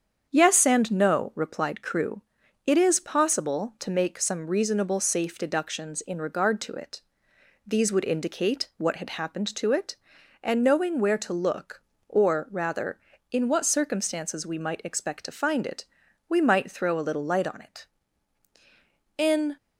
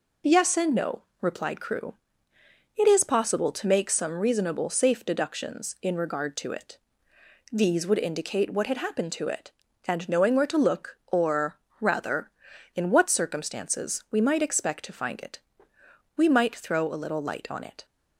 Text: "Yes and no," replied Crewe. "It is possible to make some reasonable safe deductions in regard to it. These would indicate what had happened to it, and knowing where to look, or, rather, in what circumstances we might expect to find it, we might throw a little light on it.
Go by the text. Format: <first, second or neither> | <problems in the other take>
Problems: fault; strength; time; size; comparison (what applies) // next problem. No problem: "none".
second | starts louder than the rest; strong; until 1.3 s; 8 dB // goes on to say "In"; slight; from 19.1 s on; 0.38 s long